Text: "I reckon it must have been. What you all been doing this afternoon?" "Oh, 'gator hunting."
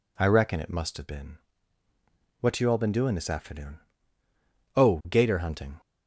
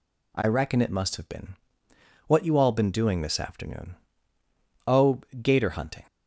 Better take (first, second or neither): neither